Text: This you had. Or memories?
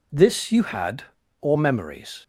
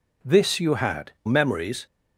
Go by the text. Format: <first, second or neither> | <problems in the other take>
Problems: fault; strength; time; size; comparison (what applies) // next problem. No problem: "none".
first | skips "Or"; at 1.2 s